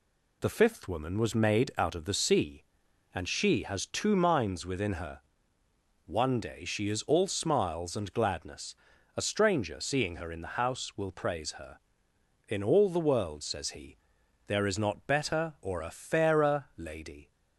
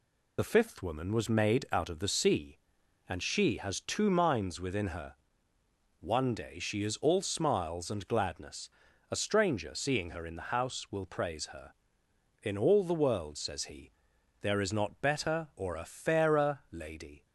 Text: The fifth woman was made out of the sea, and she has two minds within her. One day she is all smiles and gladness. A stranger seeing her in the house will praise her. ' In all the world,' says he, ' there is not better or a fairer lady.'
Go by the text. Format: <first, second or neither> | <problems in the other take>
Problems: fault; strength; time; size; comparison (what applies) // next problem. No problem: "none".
first | loses the start of "The"; at 0.3 s; 30 ms